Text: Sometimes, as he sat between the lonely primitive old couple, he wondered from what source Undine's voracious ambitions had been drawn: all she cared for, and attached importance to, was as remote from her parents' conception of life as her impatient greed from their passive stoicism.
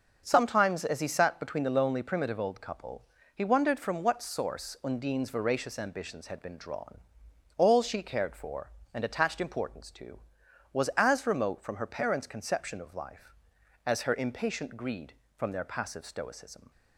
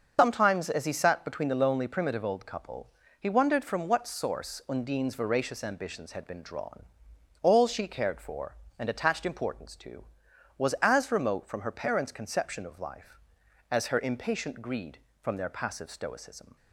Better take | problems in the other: first | loses the start of "Sometimes"; at 0.1 s; 85 ms // starts louder than the rest; until 1.1 s; 6.5 dB; also in the first

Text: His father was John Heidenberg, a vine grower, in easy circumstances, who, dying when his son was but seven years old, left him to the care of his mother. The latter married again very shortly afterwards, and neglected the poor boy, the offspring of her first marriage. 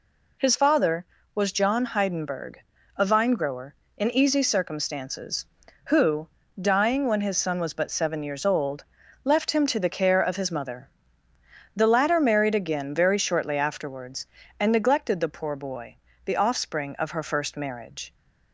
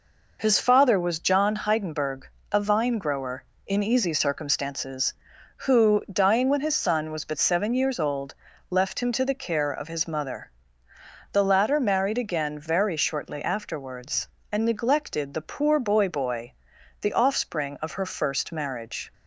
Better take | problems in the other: first | says "boy" twice; at 16.0 s

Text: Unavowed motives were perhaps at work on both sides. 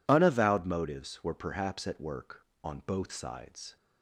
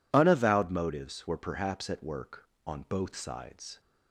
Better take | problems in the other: neither | none

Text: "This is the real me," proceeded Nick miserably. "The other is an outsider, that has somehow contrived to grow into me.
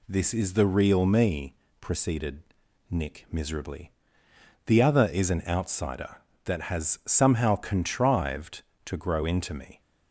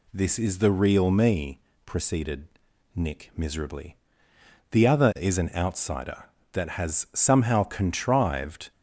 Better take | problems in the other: first | pauses between "proceeded" and "Nick"; noticeable; at 2.4 s; 0.46 s long; noticeable in the first // stops before "to grow into me"; at 8.7 s

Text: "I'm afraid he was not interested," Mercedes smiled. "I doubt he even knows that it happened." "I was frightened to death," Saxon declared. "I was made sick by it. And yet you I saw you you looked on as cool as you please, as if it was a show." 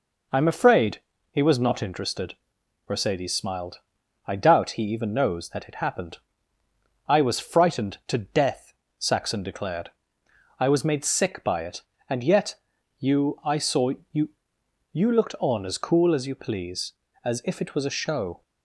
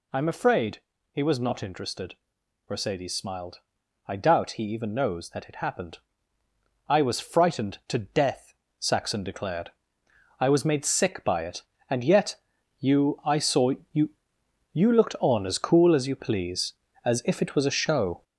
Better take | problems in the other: first | gets louder; throughout; 6.5 dB // pauses between "afraid" and "he"; slight; at 0.8 s; 0.32 s long; slight in the first // pauses between "yet" and "you"; at 12.3 s; 0.42 s long; also in the first // pauses between "saw" and "you"; slight; at 13.7 s; 0.20 s long; slight in the first // pauses between "you" and "you"; noticeable; at 14.0 s; 0.64 s long; noticeable in the first

